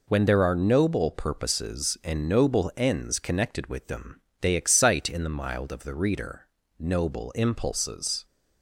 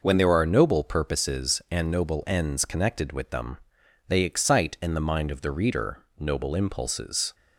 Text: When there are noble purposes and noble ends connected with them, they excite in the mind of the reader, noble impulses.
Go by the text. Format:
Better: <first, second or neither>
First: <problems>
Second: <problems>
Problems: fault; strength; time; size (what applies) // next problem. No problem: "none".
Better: second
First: says "mild" for "mind"; at 5.2 s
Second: none